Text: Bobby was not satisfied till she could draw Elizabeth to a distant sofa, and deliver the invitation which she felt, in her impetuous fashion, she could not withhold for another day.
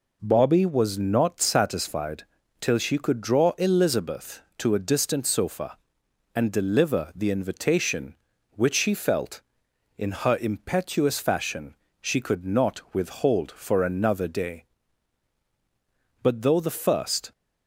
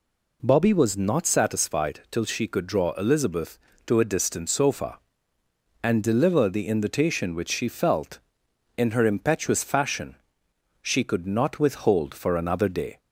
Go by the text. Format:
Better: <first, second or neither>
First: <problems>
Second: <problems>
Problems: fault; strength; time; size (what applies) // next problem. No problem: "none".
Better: second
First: pauses between "satisfied" and "till"; slight; at 2.2 s; 0.36 s long // goes on to say "But though the first"; noticeable; from 16.2 s on; 1.1 s long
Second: none